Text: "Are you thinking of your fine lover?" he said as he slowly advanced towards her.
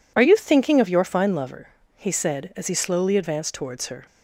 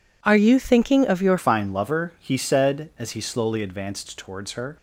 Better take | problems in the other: first | changes voice at "fine"; from 1.3 s on; 3.4 s long

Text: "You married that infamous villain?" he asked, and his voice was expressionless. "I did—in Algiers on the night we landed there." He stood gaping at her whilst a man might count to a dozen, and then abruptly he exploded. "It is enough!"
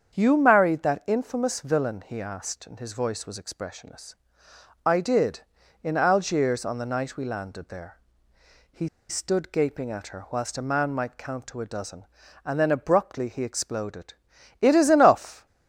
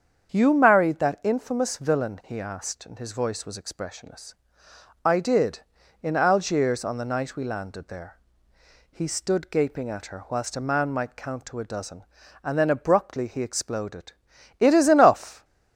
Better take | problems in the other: second | starts louder than the rest; strong; until 1.1 s; 7.5 dB; strong in the second // pauses between "He" and "stood"; slight; at 8.8 s; 0.20 s long

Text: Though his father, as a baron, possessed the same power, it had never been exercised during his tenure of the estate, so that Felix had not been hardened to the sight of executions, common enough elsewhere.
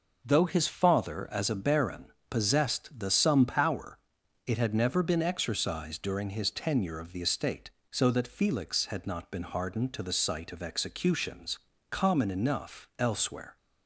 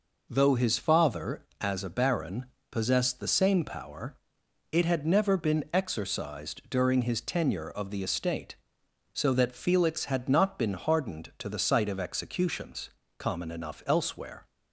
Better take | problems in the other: second | says "some" for "same"; at 3.0 s

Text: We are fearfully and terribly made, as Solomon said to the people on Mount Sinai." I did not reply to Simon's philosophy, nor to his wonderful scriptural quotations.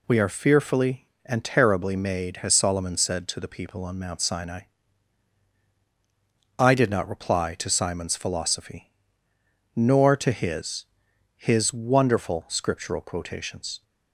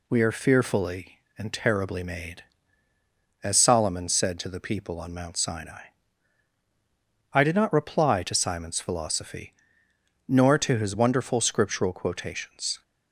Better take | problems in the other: second | says "his" twice; at 11.3 s

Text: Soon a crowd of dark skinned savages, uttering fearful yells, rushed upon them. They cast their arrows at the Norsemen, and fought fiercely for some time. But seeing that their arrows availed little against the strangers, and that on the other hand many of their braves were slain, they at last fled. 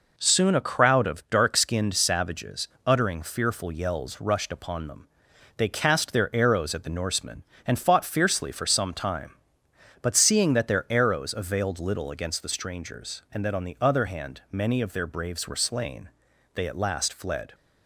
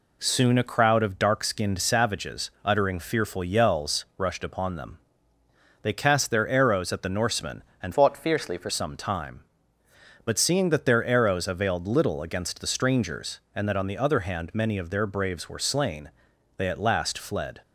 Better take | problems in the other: first | changes voice from "fought" to "for"; from 7.9 to 8.6 s; 0.7 s long

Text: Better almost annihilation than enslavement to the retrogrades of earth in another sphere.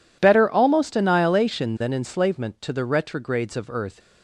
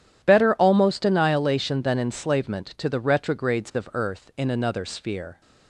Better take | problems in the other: second | stops before "in another sphere"; at 3.9 s

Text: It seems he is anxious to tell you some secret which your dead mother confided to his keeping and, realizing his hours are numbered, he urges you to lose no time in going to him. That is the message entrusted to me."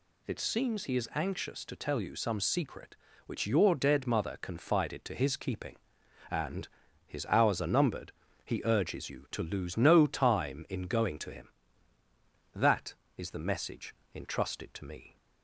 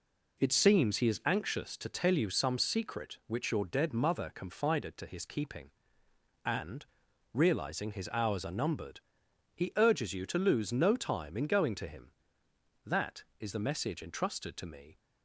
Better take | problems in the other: second | skips "realizing"; at 6.8 s // pauses between "message" and "entrusted"; slight; at 13.9 s; 0.20 s long

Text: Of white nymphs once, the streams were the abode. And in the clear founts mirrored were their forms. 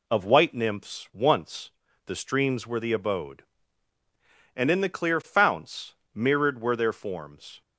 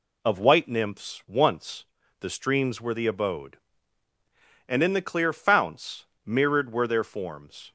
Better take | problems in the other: neither | pauses between "founts" and "mirrored"; slight; the same in both

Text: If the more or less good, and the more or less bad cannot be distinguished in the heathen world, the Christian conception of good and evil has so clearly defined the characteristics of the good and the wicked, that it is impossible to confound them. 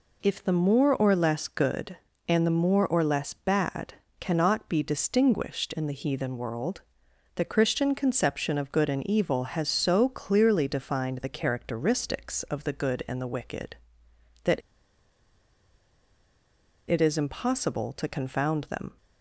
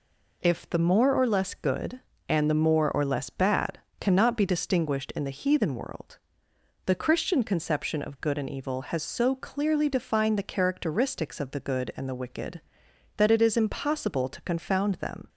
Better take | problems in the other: second | pauses between "bad" and "cannot"; slight; at 3.9 s; 0.26 s long; slight in the second // pauses between "that" and "it"; strong; at 14.6 s; 2.2 s long

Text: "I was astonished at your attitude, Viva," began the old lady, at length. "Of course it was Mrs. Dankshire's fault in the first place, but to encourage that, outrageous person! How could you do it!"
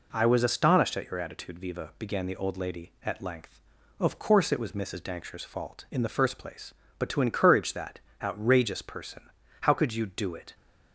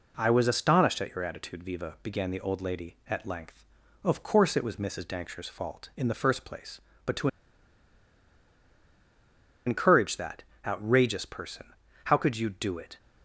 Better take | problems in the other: first | pauses between "to" and "encourage"; strong; at 7.2 s; 2.3 s long

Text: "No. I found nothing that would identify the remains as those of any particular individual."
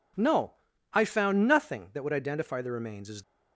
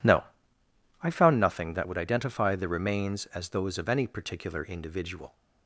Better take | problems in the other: second | stops before "those of any particular individual"; at 3.2 s

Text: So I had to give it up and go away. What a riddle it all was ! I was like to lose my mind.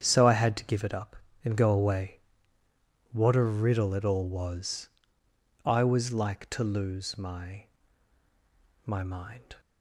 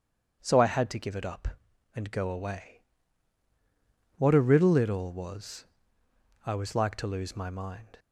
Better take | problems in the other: second | starts louder than the rest; strong; until 1.0 s; 8.5 dB // says "my" twice; at 8.8 s

